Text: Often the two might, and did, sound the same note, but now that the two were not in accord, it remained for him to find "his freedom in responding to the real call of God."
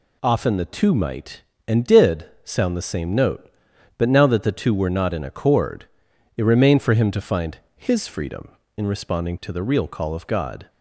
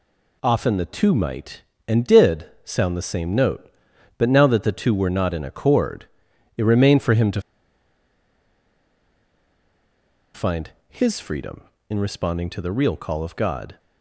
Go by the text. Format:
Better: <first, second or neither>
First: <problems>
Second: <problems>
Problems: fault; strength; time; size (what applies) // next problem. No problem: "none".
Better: first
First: pauses between "find" and "his"; slight; at 7.5 s; 0.18 s long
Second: pauses between "to" and "find"; strong; at 7.4 s; 2.9 s long // pauses between "find" and "his"; slight; at 10.7 s; 0.18 s long